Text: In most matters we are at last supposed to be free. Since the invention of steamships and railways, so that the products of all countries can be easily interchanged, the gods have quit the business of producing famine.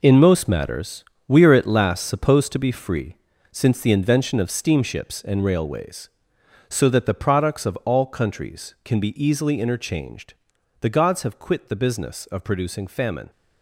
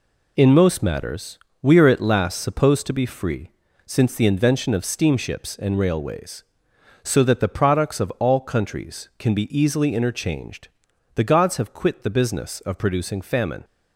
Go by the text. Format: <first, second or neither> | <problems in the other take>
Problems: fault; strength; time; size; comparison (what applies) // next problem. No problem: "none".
second | gets quieter; strong; throughout; 10 dB // pauses between "matters" and "we"; slight; at 1.0 s; 0.22 s long; slight in the second